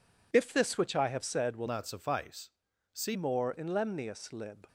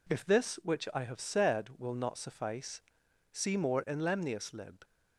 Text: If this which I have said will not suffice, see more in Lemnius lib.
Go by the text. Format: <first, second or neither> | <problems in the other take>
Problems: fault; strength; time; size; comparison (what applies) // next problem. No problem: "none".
second | changes voice from "not" to "see"; from 1.6 to 3.1 s; 1.5 s long